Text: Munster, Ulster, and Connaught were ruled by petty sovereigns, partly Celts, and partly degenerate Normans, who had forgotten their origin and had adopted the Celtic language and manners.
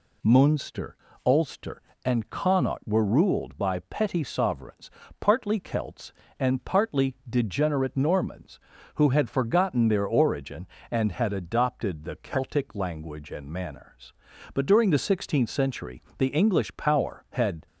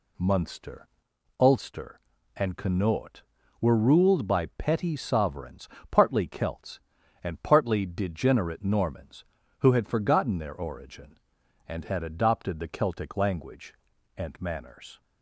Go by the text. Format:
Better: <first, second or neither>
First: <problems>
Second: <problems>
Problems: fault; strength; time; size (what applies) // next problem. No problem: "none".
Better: second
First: goes on to say "But during the sixteenth century the English power had"; strong; from 14.5 s on; 3.1 s long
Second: none